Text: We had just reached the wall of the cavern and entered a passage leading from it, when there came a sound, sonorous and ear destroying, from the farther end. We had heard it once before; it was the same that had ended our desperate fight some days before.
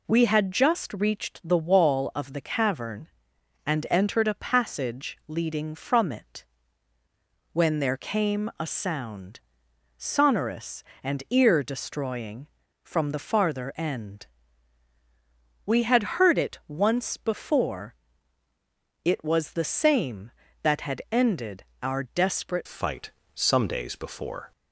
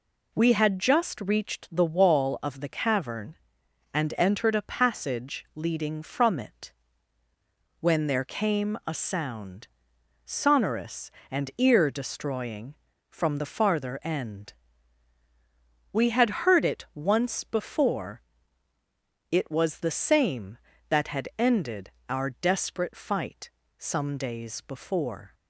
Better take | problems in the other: second | pauses between "ended" and "our"; slight; at 21.6 s; 0.18 s long; slight in the second // changes voice at "fight"; from 22.6 s on; 1.9 s long // pauses between "fight" and "some"; slight; at 23.0 s; 0.24 s long; slight in the second

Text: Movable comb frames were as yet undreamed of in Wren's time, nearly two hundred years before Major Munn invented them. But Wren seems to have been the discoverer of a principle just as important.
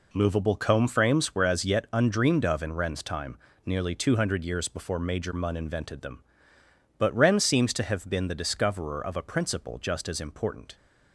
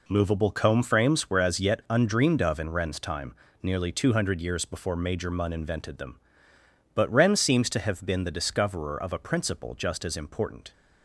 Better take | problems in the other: neither | none

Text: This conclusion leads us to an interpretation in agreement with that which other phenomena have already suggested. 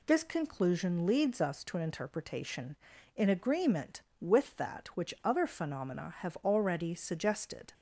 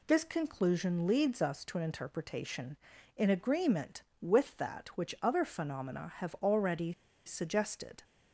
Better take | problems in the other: first | pauses between "already" and "suggested"; slight; at 6.9 s; 0.32 s long

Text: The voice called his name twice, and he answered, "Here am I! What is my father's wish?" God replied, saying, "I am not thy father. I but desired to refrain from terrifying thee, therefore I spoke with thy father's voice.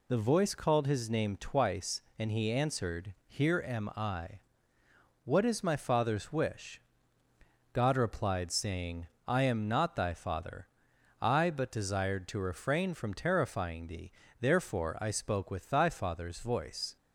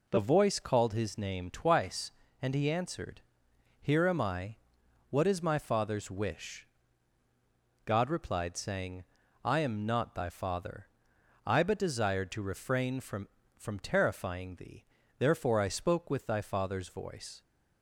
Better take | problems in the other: first | says "from" twice; at 13.5 s

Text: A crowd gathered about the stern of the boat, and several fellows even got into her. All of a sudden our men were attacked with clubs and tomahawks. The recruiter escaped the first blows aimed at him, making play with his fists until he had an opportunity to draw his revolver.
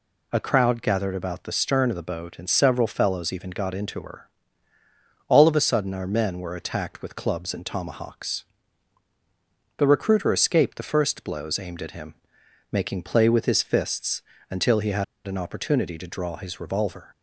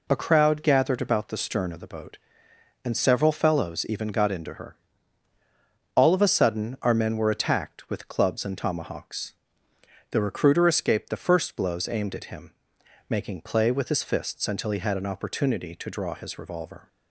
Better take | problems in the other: second | pauses between "fists" and "until"; slight; at 14.2 s; 0.28 s long // pauses between "had" and "an"; slight; at 15.0 s; 0.21 s long

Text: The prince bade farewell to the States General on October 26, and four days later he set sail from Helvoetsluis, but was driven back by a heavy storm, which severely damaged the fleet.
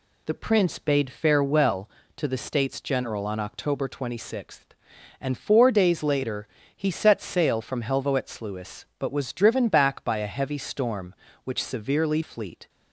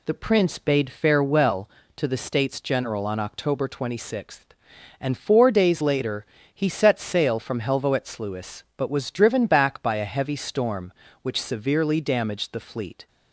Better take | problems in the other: second | pauses between "later" and "he"; slight; at 6.4 s; 0.30 s long; slight in the second // skips "damaged the"; at 12.2 s

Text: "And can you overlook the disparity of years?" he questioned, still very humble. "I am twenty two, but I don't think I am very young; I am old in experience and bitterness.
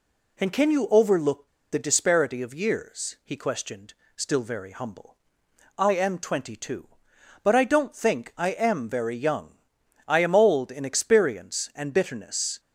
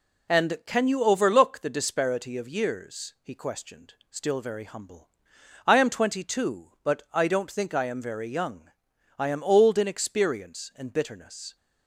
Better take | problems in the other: second | pauses between "overlook" and "the"; slight; at 1.4 s; 0.23 s long

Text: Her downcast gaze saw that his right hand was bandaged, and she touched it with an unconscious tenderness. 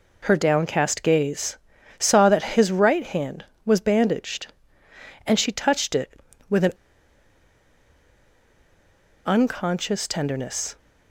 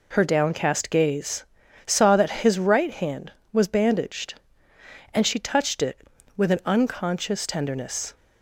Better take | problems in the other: second | pauses between "gaze" and "saw"; at 1.5 s; 0.42 s long; also in the second // pauses between "an" and "unconscious"; strong; at 6.7 s; 2.5 s long

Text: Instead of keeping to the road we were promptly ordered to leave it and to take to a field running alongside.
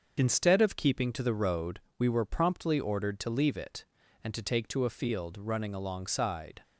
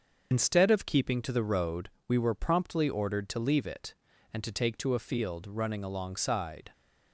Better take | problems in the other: first | loses the start of "Instead"; at 0.3 s; 40 ms // starts louder than the rest; until 1.3 s; 6.5 dB; also in the first // pauses between "road" and "we"; slight; at 1.8 s; 0.18 s long; slight in the first

